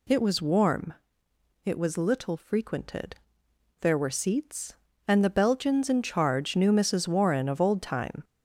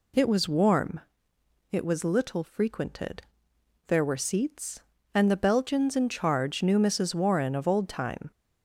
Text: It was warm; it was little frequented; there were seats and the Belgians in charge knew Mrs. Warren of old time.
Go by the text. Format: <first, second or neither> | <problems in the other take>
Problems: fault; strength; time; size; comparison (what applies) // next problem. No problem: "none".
second | gets louder; throughout; 3.5 dB